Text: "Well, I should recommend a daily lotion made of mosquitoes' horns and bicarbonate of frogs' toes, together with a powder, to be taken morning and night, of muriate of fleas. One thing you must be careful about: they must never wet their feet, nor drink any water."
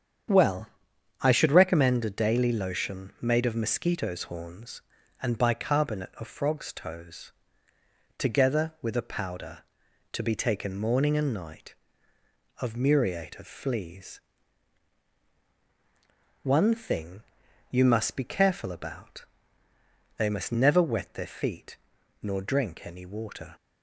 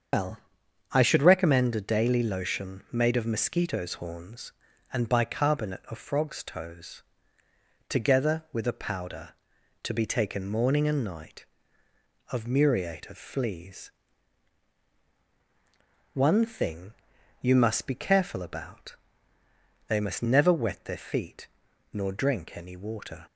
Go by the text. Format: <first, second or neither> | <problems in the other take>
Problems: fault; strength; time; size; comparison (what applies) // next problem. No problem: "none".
first | loses the start of "Well"; at 0.1 s; 140 ms // starts louder than the rest; strong; until 1.6 s; 7.5 dB; strong in the first // pauses between "thing" and "you"; noticeable; at 16.9 s; 0.48 s long; noticeable in the first